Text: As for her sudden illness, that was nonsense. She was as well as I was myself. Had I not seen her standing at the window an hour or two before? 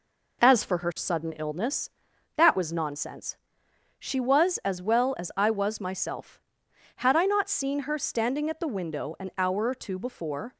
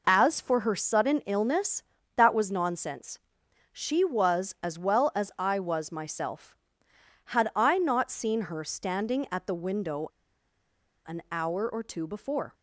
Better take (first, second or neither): first